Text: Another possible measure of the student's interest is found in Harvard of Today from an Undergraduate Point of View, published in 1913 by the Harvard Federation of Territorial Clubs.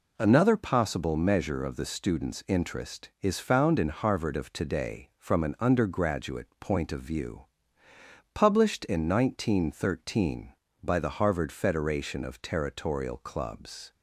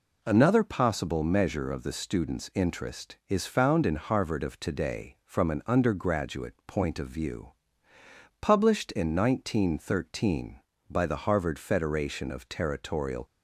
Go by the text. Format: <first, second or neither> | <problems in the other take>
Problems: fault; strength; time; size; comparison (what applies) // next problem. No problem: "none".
first | stops before "Clubs"; at 13.2 s